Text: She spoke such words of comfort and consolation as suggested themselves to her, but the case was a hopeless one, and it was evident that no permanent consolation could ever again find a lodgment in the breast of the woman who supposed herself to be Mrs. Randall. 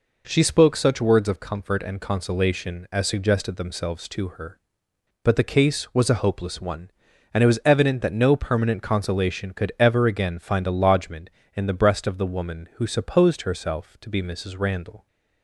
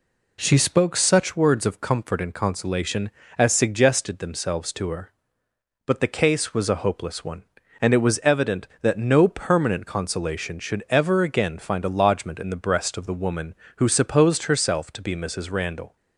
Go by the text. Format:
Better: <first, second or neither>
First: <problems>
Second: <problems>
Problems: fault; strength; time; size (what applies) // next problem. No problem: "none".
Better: first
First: none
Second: says "should" for "could"; at 10.5 s